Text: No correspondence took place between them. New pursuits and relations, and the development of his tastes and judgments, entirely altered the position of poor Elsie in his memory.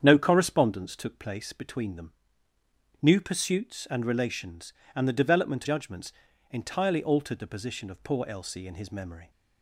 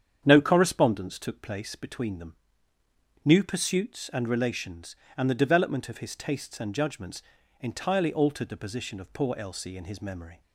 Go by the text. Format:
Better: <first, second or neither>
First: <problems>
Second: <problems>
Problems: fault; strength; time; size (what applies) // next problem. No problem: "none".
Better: second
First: starts louder than the rest; strong; until 1.0 s; 8 dB // skips "of his tastes and"; at 5.6 s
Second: starts louder than the rest; strong; until 1.2 s; 8.5 dB